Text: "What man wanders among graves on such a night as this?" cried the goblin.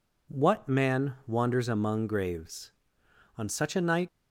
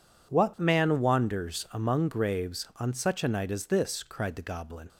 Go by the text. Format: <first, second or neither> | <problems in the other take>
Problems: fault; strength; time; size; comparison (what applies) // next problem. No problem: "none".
second | stops before "as this cried the goblin"; at 4.0 s